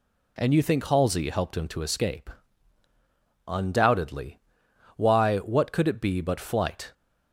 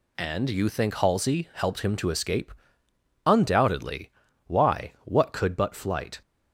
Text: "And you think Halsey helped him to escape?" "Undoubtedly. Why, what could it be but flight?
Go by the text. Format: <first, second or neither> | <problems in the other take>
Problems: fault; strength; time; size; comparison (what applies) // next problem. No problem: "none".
first | skips "it be"; at 5.5 s